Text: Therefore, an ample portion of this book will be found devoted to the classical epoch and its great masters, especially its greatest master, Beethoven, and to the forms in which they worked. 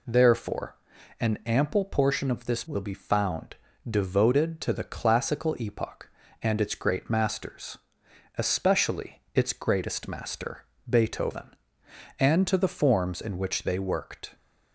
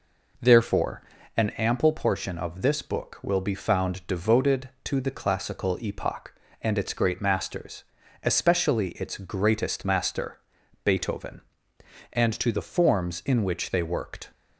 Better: second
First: skips "book"; at 2.6 s // pauses between "found" and "devoted"; slight; at 3.5 s; 0.34 s long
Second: none

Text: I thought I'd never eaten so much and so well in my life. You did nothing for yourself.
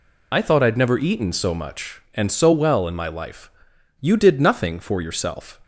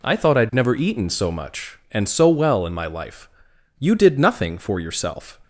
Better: second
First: loses the start of "I"; at 0.3 s; 35 ms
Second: none

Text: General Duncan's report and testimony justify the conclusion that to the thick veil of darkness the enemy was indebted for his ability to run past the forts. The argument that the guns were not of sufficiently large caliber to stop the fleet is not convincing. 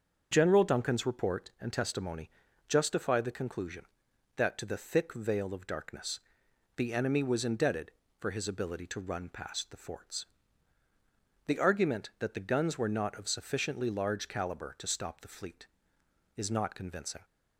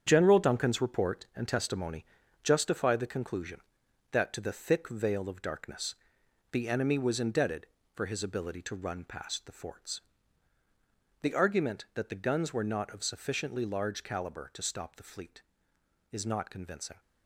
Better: first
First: starts louder than the rest; until 1.3 s; 7 dB // pauses between "testimony" and "justify"; slight; at 2.3 s; 0.36 s long // pauses between "darkness" and "the"; noticeable; at 6.2 s; 0.56 s long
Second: gets quieter; strong; throughout; 8.5 dB // starts louder than the rest; strong; until 1.0 s; 8 dB // pauses between "testimony" and "justify"; slight; at 2.0 s; 0.36 s long // pauses between "darkness" and "the"; noticeable; at 5.9 s; 0.56 s long

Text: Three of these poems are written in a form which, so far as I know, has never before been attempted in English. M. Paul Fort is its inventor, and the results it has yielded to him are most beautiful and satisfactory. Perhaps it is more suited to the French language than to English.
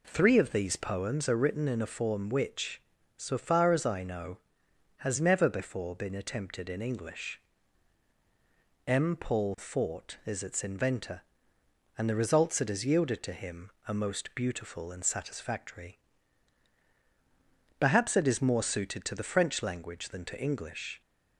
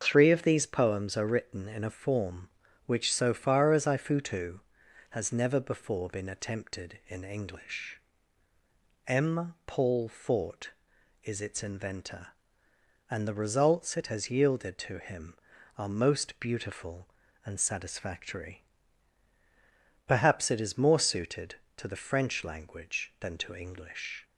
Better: first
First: none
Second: starts louder than the rest; until 1.0 s; 7 dB // says "futu" for "know"; at 3.9 s

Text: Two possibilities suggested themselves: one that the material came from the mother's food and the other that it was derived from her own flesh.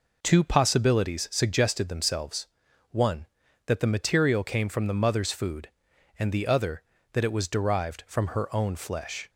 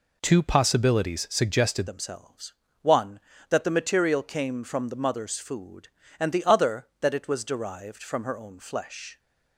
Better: first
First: none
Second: changes voice at "themselves"; from 1.8 s on; 7.3 s long

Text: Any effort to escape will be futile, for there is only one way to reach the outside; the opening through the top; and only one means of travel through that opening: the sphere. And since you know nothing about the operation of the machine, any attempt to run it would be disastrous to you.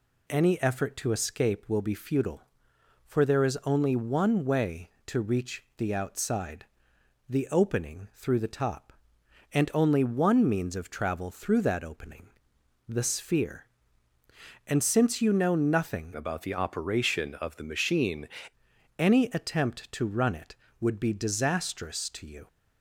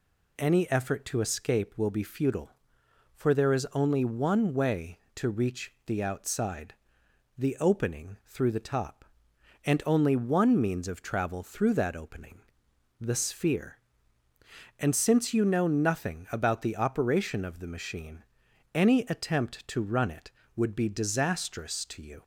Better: second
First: changes voice from "about" to "machine"; from 16.1 to 18.2 s; 2.1 s long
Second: none

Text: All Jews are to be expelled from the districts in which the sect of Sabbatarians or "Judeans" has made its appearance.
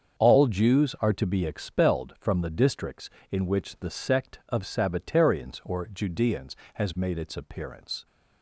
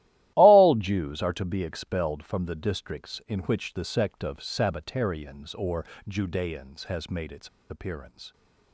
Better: first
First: starts louder than the rest; strong; until 1.2 s; 7 dB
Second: starts louder than the rest; strong; until 1.3 s; 15 dB // pauses between "or" and "Judeans"; slight; at 5.8 s; 0.22 s long // pauses between "its" and "appearance"; slight; at 7.4 s; 0.21 s long

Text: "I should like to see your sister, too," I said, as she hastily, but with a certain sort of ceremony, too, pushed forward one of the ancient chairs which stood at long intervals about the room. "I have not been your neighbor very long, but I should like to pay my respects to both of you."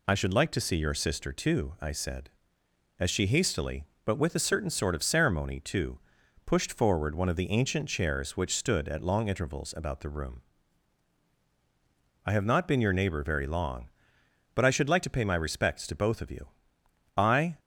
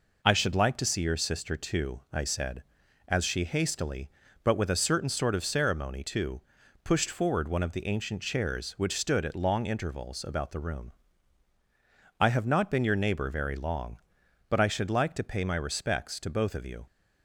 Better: second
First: goes on to say "I"; slight; from 17.1 s on; 0.42 s long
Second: none

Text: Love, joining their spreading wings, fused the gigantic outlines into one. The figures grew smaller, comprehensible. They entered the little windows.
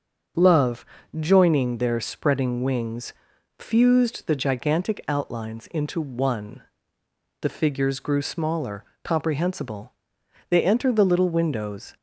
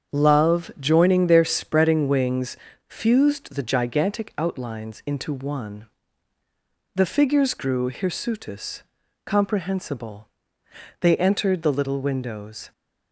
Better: first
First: starts louder than the rest; until 1.7 s; 6.5 dB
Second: starts louder than the rest; strong; until 1.2 s; 7.5 dB // says "hirsutus" for "smaller"; at 7.9 s

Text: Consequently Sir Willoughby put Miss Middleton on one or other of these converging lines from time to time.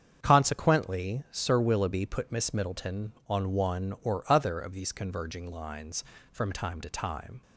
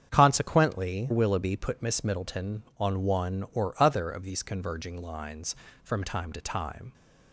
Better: first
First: starts louder than the rest; strong; until 1.2 s; 7.5 dB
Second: starts louder than the rest; strong; until 1.1 s; 8 dB // skips "Sir"; at 1.1 s

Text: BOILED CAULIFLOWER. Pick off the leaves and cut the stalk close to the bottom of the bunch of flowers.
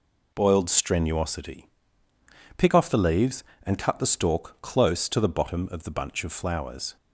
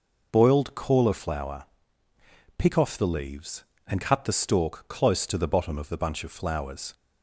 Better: second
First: says "Strenuosity" for "CAULIFLOWER"; at 0.6 s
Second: none

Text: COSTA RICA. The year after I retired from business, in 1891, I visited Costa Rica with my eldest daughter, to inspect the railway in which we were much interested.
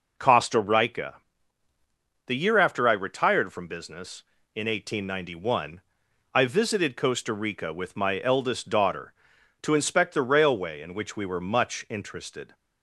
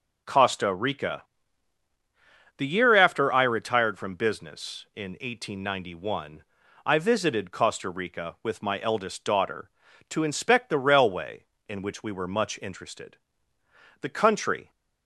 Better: first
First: none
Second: goes on to say "The country"; noticeable; from 13.9 s on; 0.70 s long

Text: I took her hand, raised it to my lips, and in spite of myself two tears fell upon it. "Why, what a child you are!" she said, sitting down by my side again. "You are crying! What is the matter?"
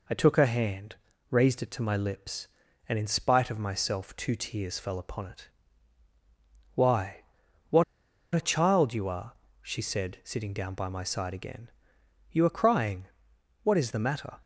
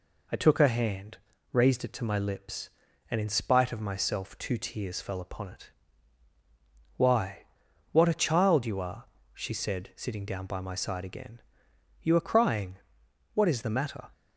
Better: second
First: pauses between "what" and "a"; noticeable; at 7.8 s; 0.51 s long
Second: none

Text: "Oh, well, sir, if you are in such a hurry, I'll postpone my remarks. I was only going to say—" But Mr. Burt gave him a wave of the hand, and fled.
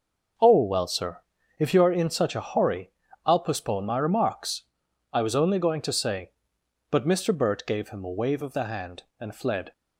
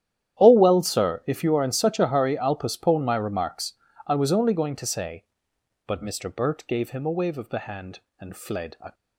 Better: first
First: none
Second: starts louder than the rest; strong; until 1.4 s; 11 dB // goes on to say "A"; slight; from 8.7 s on; 0.14 s long

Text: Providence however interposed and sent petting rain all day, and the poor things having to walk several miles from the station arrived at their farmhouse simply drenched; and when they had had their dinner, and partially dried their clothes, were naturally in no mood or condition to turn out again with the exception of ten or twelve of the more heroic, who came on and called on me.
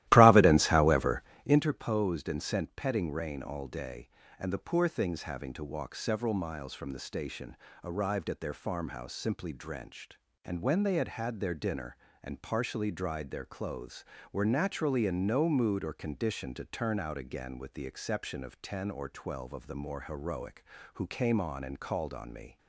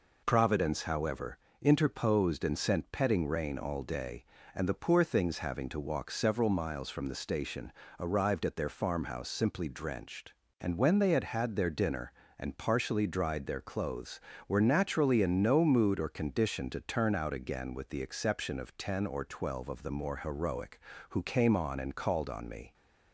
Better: second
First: starts louder than the rest; strong; until 1.6 s; 15.5 dB // pauses between "however" and "interposed"; slight; at 1.2 s; 0.24 s long // pauses between "station" and "arrived"; slight; at 7.5 s; 0.28 s long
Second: pauses between "however" and "interposed"; slight; at 1.3 s; 0.24 s long // pauses between "station" and "arrived"; slight; at 7.7 s; 0.28 s long

